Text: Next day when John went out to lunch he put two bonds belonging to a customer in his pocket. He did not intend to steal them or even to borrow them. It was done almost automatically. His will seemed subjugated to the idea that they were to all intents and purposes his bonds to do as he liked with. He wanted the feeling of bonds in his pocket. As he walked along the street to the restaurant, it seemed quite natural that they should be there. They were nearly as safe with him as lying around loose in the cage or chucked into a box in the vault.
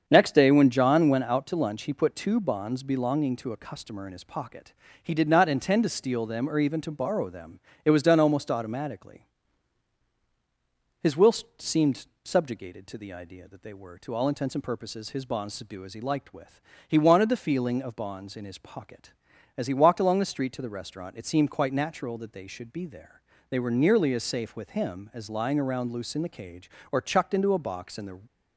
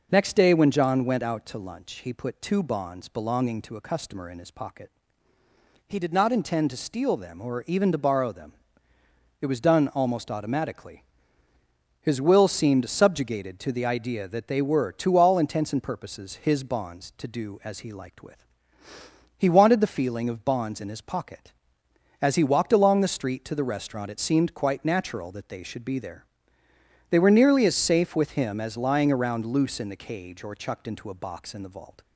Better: second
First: starts louder than the rest; strong; until 1.1 s; 7 dB // pauses between "will" and "seemed"; slight; at 11.3 s; 0.24 s long // pauses between "seemed" and "subjugated"; slight; at 12.0 s; 0.16 s long // stops before "vault"; at 28.2 s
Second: none

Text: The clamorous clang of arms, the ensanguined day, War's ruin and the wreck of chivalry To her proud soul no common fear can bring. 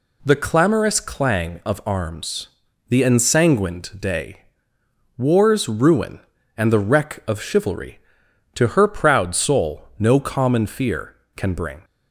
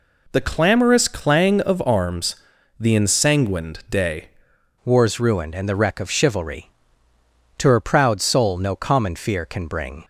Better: first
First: none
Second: changes voice at "War's"; from 4.8 s on; 5.2 s long

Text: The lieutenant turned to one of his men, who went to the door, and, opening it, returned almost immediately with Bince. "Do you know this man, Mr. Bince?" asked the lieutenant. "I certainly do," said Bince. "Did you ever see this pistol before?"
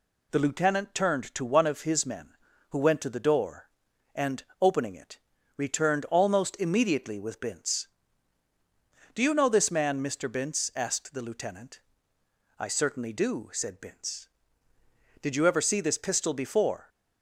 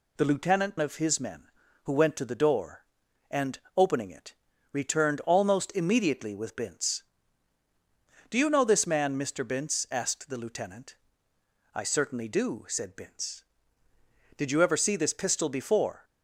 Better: first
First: none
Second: skips "turned to one"; at 0.7 s

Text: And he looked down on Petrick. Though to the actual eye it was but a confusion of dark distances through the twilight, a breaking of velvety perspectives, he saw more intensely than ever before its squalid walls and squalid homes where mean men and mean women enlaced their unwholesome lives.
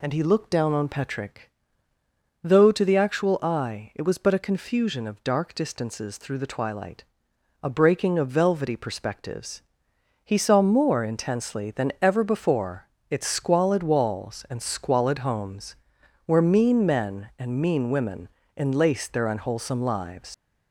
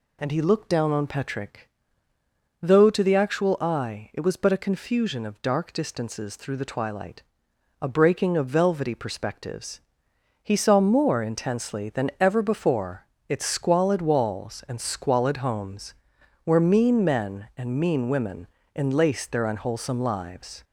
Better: second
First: pauses between "before" and "its"; slight; at 12.8 s; 0.24 s long // pauses between "homes" and "where"; noticeable; at 15.7 s; 0.50 s long // pauses between "women" and "enlaced"; slight; at 18.2 s; 0.28 s long // leaves "lives" unfinished; at 20.3 s; 110 ms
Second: pauses between "before" and "its"; slight; at 13.0 s; 0.24 s long // pauses between "homes" and "where"; noticeable; at 15.9 s; 0.50 s long // pauses between "women" and "enlaced"; slight; at 18.4 s; 0.28 s long

